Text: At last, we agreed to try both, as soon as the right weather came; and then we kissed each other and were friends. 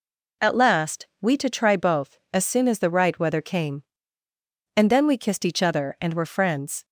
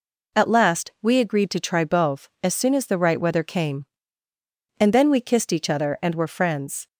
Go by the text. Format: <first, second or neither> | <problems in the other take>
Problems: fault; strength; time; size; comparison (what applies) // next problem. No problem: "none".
second | skips "agreed"; at 1.3 s